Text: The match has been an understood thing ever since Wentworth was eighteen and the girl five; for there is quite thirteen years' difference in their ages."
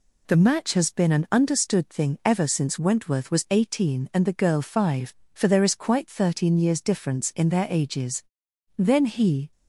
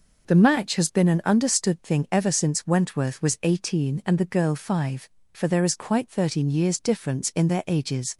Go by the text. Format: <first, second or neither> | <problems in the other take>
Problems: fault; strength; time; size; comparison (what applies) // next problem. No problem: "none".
second | goes on to say "Then he"; noticeable; from 8.7 s on; 0.76 s long